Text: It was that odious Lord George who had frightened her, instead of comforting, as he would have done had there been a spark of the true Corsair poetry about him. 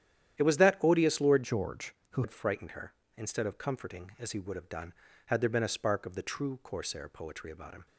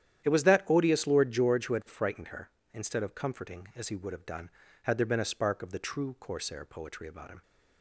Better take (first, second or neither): second